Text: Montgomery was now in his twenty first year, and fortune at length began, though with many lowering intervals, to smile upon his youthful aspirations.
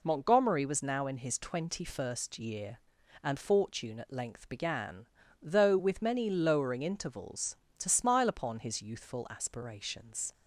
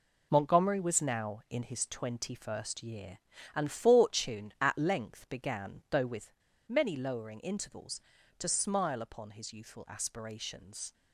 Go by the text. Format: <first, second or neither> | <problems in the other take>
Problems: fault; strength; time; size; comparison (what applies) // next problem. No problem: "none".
first | pauses between "with" and "many"; at 6.3 s; 0.37 s long